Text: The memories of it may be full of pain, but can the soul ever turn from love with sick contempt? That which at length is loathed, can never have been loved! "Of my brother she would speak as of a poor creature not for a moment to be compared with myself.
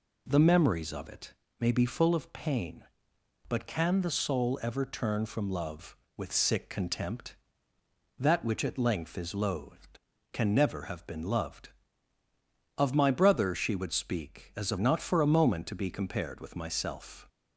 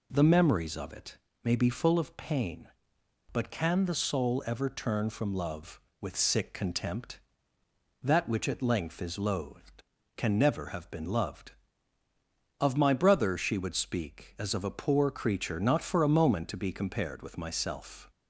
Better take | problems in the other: second | pauses between "it" and "may"; slight; at 1.3 s; 0.28 s long; slight in the second // skips "a poor creature"; at 14.7 s

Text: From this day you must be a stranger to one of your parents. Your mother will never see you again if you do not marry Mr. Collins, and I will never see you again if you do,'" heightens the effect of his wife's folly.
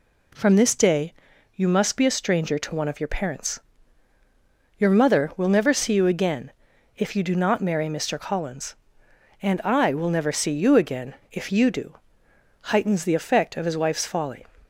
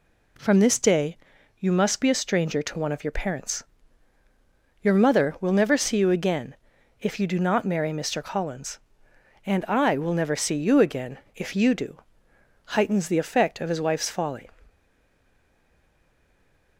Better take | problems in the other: first | pauses between "day" and "you"; at 1.1 s; 0.42 s long; also in the first // pauses between "again" and "if"; noticeable; at 6.5 s; 0.46 s long; noticeable in the first // pauses between "again" and "if"; slight; at 11.1 s; 0.18 s long; slight in the first // stays silent after the last word; from 14.6 s on; 2.1 s long

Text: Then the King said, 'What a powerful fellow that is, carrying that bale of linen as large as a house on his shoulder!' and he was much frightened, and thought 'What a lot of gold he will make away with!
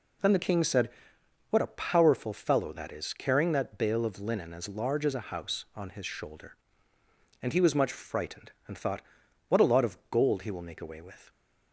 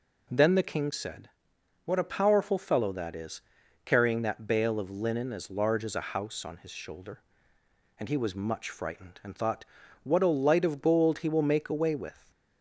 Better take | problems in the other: first | pauses between "thought" and "What"; at 9.6 s; 0.38 s long; noticeable in the first // says "light" for "lot"; at 10.2 s

